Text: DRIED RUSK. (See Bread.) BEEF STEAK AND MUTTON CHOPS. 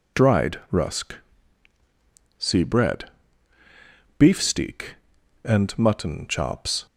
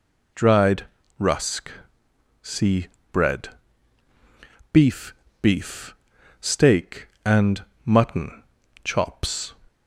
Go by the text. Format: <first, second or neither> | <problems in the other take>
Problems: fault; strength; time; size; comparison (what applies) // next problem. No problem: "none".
first | pauses between "DRIED" and "RUSK"; slight; at 0.8 s; 0.34 s long // pauses between "See" and "Bread"; slight; at 2.8 s; 0.26 s long // says "BEEF" twice; at 5.4 s // pauses between "AND" and "MUTTON"; slight; at 7.6 s; 0.20 s long // pauses between "MUTTON" and "CHOPS"; at 8.4 s; 0.40 s long